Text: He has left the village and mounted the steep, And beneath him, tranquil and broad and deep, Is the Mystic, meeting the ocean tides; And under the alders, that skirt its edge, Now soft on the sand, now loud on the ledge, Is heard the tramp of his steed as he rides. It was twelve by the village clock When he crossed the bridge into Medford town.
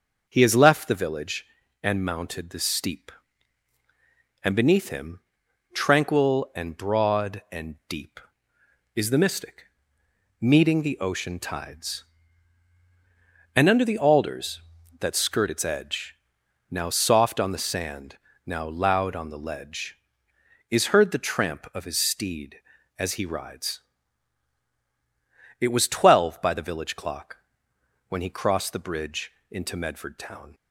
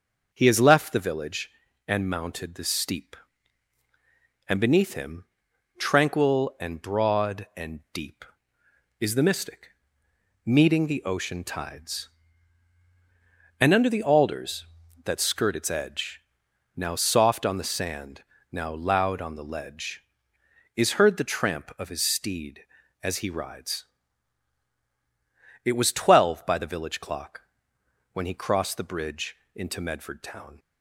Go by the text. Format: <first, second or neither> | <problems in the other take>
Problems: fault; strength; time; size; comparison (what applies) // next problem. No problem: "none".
neither | pauses between "clock" and "When"; noticeable; the same in both // pauses between "bridge" and "into"; slight; the same in both